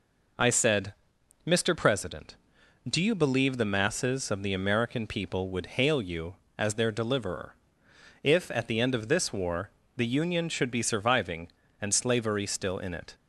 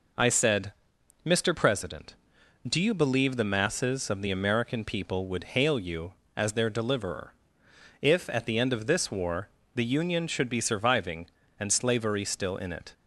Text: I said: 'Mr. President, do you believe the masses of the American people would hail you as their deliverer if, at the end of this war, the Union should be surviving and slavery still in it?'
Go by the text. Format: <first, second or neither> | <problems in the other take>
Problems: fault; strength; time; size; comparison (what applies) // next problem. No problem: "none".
neither | pauses between "deliverer" and "if"; noticeable; the same in both